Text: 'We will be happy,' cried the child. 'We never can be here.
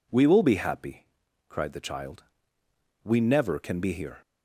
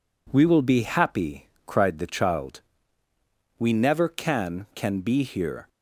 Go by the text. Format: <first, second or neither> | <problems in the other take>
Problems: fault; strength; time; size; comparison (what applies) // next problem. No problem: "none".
first | says "can" twice; at 4.7 s